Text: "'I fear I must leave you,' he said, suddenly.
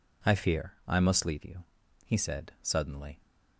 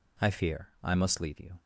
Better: first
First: none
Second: stops before "he said suddenly"; at 1.5 s

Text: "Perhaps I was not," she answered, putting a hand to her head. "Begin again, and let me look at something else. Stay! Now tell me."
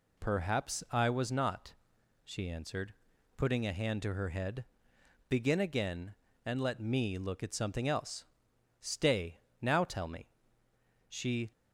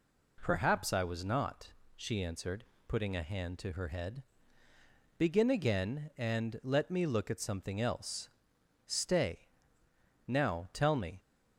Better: second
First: goes on to say "She"; slight; from 11.0 s on; 0.44 s long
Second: none

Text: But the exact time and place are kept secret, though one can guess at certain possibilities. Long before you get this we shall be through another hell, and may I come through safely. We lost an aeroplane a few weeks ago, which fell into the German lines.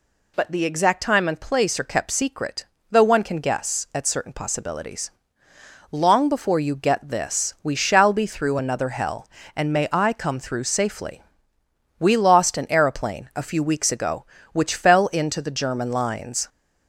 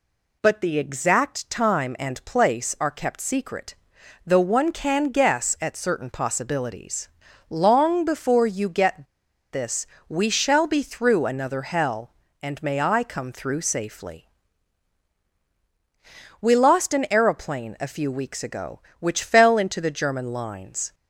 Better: first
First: none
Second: pauses between "get" and "this"; noticeable; at 9.0 s; 0.47 s long // pauses between "this" and "we"; slight; at 9.8 s; 0.22 s long

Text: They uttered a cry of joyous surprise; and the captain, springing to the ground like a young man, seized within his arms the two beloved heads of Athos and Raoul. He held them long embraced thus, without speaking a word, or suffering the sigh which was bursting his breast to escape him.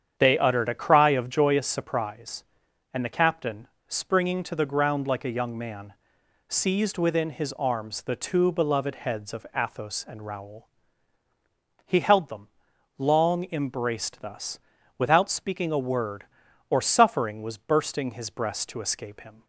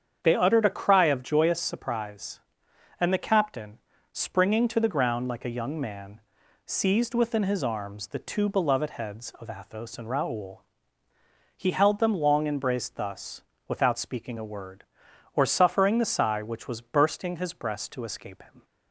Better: second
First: starts louder than the rest; strong; until 1.1 s; 8.5 dB // pauses between "them" and "long"; noticeable; at 12.4 s; 0.52 s long // skips "the sigh which"; at 17.4 s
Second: starts louder than the rest; strong; until 1.2 s; 7.5 dB

